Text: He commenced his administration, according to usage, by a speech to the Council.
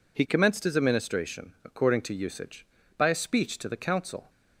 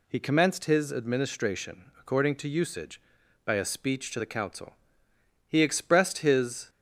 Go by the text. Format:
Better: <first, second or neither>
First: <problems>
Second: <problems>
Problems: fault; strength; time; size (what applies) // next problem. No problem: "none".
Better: first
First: none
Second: goes on to say "He expressed his"; noticeable; from 5.4 s on; 1.2 s long